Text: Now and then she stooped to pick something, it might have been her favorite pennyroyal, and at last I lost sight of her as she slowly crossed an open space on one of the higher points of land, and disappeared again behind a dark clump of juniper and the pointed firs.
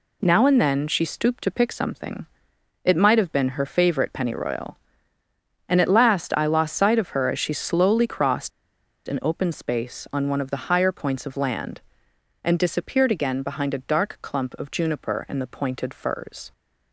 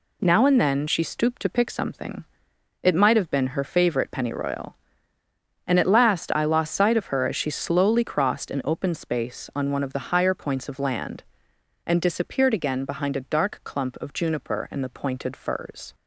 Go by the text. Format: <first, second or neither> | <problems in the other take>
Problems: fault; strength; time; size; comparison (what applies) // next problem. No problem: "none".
second | pauses between "crossed" and "an"; noticeable; at 8.5 s; 0.57 s long